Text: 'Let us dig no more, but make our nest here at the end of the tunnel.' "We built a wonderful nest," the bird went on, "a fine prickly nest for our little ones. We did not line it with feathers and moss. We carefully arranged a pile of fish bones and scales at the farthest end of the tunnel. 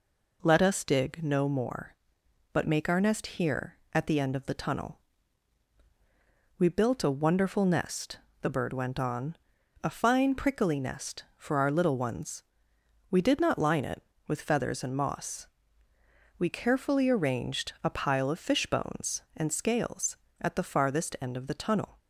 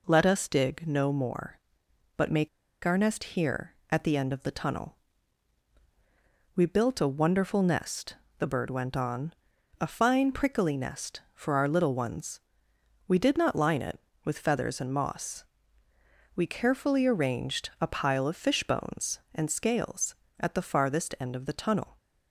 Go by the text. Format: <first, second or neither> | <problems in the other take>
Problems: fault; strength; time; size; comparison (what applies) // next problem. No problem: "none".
first | pauses between "make" and "our"; at 2.4 s; 0.36 s long